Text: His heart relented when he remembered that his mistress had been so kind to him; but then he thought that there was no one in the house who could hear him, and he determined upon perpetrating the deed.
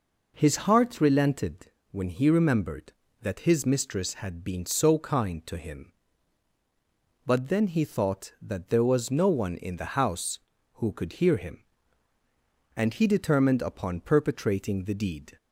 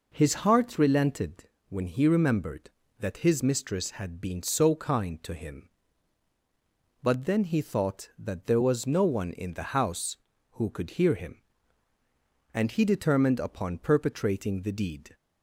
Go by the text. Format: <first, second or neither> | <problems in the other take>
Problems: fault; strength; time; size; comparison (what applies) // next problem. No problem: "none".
neither | pauses between "relented" and "when"; slight; the same in both